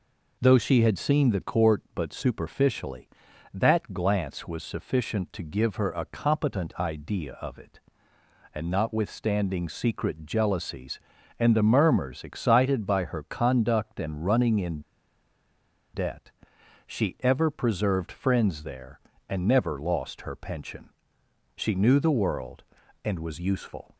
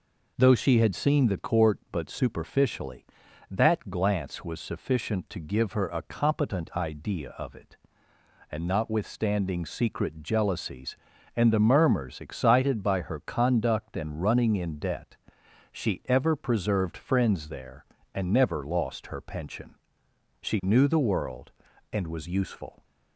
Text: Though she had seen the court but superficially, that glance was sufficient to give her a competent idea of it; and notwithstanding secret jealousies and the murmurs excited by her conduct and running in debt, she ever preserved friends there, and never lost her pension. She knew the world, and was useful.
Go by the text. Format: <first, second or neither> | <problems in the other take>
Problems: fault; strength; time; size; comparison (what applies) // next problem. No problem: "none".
second | pauses between "in" and "debt"; at 14.7 s; 1.1 s long